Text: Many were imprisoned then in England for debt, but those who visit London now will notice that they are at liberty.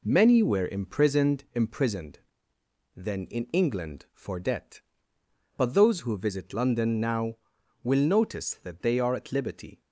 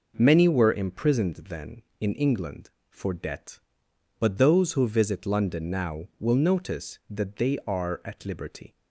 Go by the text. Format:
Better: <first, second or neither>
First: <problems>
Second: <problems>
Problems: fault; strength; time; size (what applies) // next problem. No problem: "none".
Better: second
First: says "imprisoned" twice; at 1.5 s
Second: none